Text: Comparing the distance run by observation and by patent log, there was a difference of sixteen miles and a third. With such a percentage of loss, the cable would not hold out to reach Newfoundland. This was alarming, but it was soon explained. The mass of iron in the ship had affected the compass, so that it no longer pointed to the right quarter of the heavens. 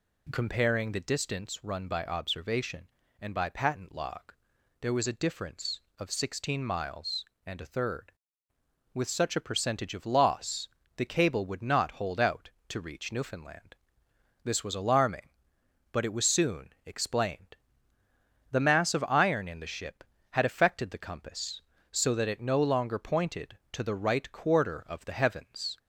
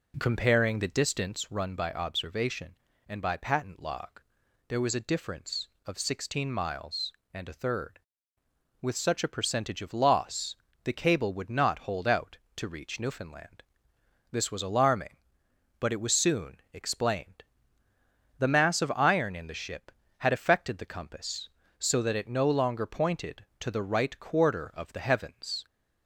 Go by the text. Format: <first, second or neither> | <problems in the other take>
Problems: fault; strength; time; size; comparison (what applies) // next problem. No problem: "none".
first | starts louder than the rest; until 1.7 s; 3.5 dB